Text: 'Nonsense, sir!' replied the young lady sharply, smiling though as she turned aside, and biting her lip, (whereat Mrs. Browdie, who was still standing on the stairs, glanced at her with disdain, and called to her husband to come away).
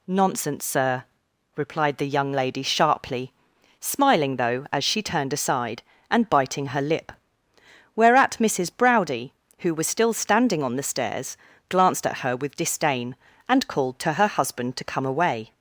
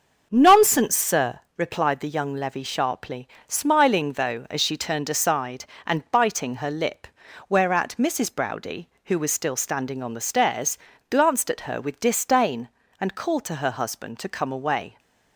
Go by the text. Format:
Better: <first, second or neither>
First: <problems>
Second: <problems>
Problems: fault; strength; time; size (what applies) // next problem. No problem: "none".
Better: first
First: none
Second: starts louder than the rest; until 1.3 s; 6.5 dB // says "levy" for "lady"; at 2.3 s